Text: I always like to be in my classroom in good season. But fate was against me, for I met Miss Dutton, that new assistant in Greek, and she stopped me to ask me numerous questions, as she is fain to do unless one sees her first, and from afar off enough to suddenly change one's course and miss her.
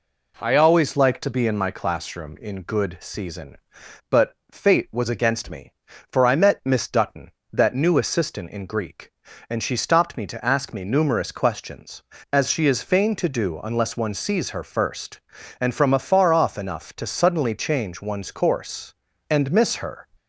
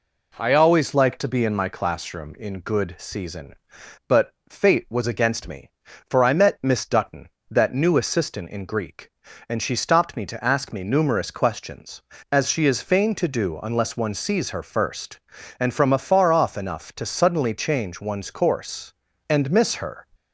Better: neither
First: pauses between "But" and "fate"; slight; at 4.3 s; 0.16 s long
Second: pauses between "But" and "fate"; slight; at 4.3 s; 0.16 s long

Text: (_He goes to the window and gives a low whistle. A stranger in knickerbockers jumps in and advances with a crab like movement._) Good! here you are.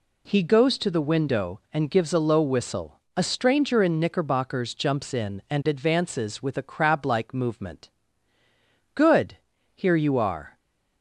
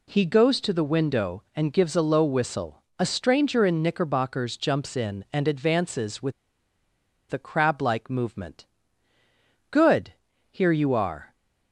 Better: first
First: none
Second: pauses between "with" and "a"; at 6.3 s; 0.98 s long

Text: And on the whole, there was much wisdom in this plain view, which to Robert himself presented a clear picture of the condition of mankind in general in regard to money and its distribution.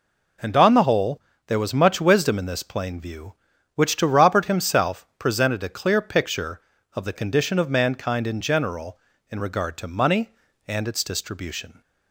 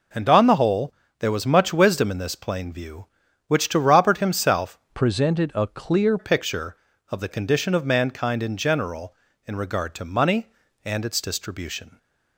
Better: first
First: none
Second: changes voice from "presented" to "clear"; from 4.9 to 6.1 s; 1.2 s long

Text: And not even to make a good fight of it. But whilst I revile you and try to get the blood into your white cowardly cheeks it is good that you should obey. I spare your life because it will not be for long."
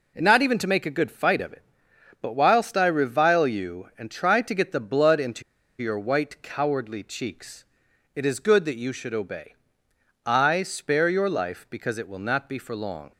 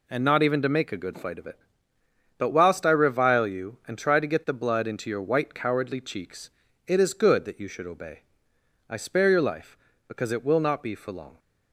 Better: second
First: pauses between "into" and "your"; at 5.4 s; 0.38 s long // pauses between "cheeks" and "it"; noticeable; at 7.6 s; 0.50 s long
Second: pauses between "cheeks" and "it"; slight; at 6.5 s; 0.36 s long

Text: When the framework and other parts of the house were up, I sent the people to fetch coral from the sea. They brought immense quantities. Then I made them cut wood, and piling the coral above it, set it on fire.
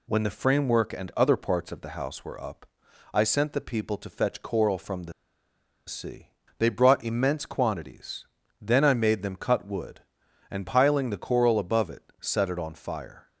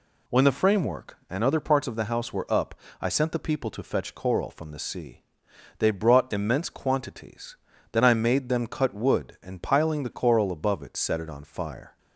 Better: second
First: pauses between "the" and "sea"; noticeable; at 5.1 s; 0.74 s long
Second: none

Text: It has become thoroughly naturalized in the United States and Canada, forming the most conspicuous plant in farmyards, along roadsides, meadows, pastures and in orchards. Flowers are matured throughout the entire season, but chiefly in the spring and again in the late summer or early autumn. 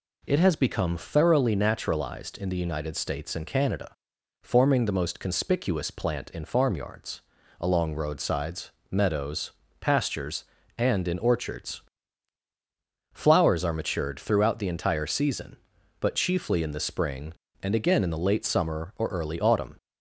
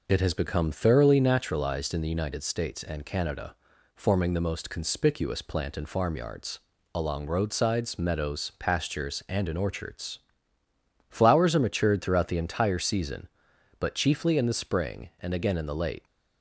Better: first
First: none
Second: stops before "summer or early autumn"; at 16.0 s

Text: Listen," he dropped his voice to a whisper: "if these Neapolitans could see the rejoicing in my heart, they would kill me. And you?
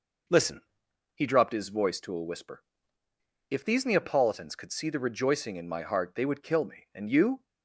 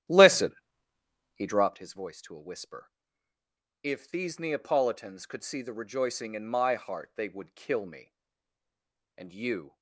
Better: first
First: none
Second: starts louder than the rest; strong; until 1.8 s; 12.5 dB

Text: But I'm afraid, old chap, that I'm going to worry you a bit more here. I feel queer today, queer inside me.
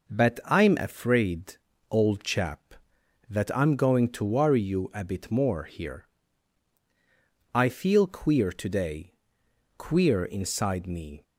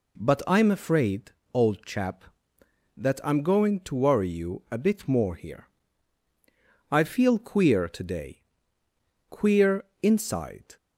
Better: first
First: none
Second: pauses between "queer" and "inside"; slight; at 9.8 s; 0.18 s long // stops before "me"; at 10.7 s

